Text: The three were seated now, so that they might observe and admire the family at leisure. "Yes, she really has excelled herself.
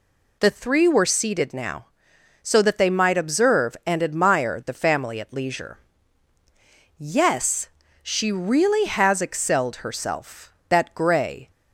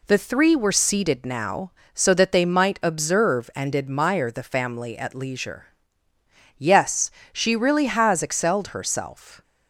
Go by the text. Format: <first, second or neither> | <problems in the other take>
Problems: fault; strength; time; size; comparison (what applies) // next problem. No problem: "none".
second | goes on to say "That grey"; noticeable; from 10.6 s on; 0.80 s long